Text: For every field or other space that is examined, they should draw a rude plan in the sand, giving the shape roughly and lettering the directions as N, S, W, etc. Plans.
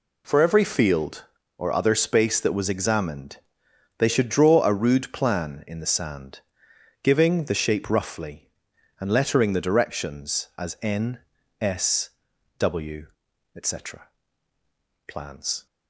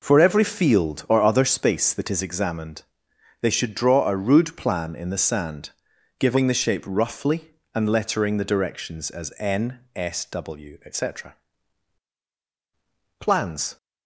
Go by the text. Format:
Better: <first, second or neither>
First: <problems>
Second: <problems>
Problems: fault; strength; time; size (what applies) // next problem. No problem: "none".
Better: second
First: says "was" for "is"; at 2.5 s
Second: none